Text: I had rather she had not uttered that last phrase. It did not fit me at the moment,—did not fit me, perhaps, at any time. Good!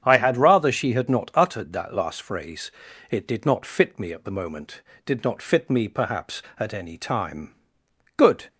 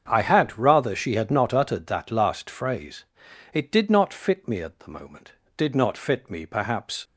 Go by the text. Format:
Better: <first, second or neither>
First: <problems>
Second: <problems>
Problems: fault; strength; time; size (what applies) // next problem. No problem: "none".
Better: first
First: starts louder than the rest; strong; until 1.0 s; 8 dB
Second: starts louder than the rest; strong; until 1.0 s; 7.5 dB // stops before "at any time Good"; at 7.0 s